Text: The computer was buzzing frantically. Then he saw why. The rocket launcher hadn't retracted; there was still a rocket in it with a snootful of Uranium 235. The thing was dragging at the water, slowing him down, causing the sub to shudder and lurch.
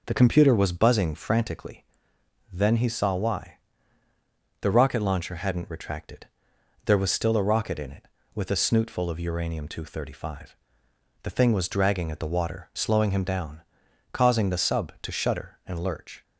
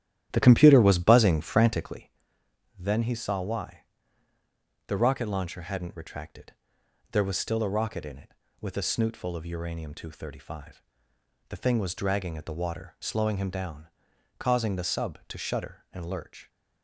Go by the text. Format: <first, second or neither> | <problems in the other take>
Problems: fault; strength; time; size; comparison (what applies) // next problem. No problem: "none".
first | starts louder than the rest; strong; until 2.1 s; 12 dB